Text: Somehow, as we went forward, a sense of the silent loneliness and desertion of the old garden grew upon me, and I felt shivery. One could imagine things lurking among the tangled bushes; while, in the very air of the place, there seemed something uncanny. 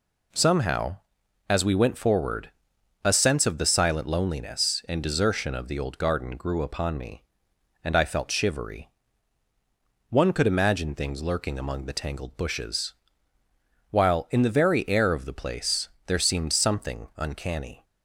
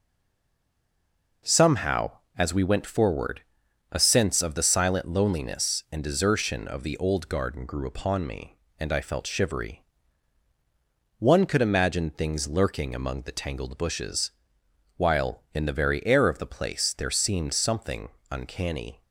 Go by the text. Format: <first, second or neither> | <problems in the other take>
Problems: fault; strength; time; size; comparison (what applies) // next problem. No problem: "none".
first | stays silent before the first word; noticeable; until 1.4 s; 1.4 s long // pauses between "something" and "uncanny"; slight; at 18.0 s; 0.22 s long